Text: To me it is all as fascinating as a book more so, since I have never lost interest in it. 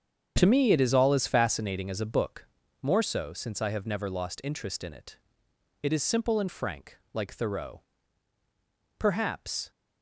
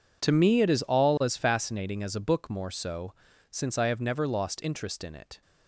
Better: second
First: starts louder than the rest; strong; until 1.3 s; 7.5 dB // pauses between "book" and "more"; at 2.4 s; 0.38 s long // goes on to say "It is simple and frank like Thoreau Perhaps"; strong; from 5.8 s on; 3.8 s long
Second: none

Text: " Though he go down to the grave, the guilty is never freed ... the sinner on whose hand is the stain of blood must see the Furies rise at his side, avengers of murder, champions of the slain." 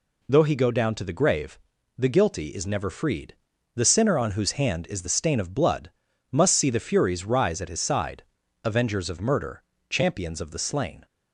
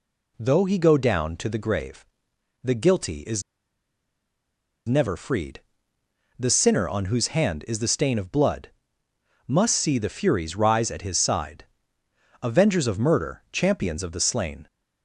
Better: first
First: pauses between "blood" and "must"; at 5.9 s; 0.38 s long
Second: pauses between "is" and "never"; strong; at 3.4 s; 1.4 s long // pauses between "blood" and "must"; noticeable; at 8.7 s; 0.76 s long

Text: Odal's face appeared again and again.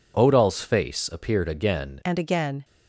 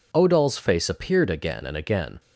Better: second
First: changes voice at "and"; from 2.0 s on; 0.6 s long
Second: none

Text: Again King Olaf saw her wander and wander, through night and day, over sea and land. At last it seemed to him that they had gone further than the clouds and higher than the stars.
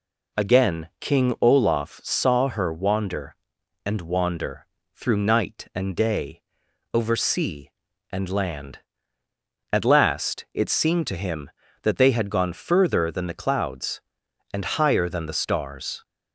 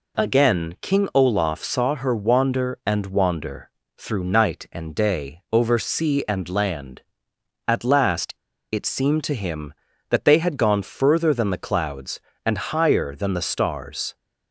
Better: first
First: none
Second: pauses between "last" and "it"; at 8.3 s; 0.40 s long

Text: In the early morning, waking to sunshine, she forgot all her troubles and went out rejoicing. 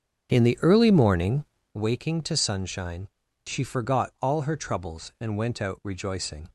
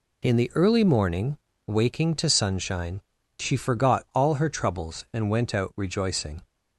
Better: second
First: starts louder than the rest; strong; until 1.7 s; 8 dB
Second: none

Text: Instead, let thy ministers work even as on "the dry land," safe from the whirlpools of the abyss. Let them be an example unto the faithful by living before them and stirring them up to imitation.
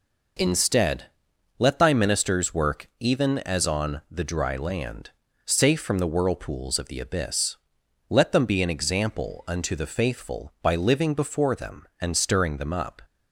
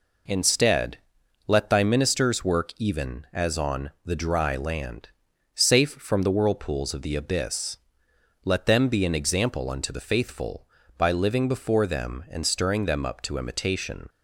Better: second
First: stops before "to imitation"; at 13.0 s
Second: none

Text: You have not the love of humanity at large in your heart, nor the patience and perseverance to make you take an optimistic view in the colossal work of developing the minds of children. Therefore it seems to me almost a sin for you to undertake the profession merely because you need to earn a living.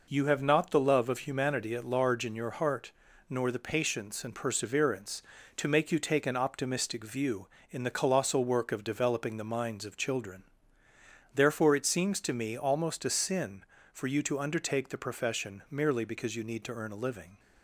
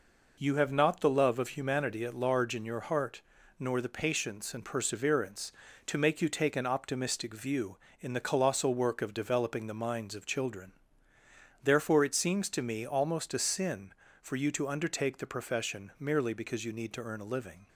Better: neither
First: none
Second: none

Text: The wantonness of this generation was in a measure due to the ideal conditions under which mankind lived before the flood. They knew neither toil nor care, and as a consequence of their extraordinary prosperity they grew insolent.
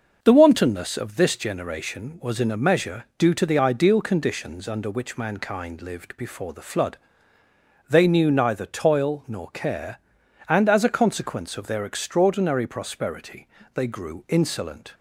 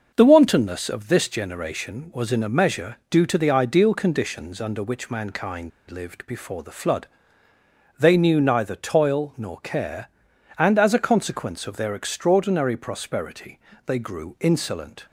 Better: first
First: starts louder than the rest; noticeable; until 1.2 s; 6 dB // pauses between "prosperity" and "they"; slight; at 13.4 s; 0.30 s long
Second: starts louder than the rest; noticeable; until 1.1 s; 6 dB // pauses between "mankind" and "lived"; slight; at 5.7 s; 0.19 s long // pauses between "prosperity" and "they"; slight; at 13.5 s; 0.30 s long

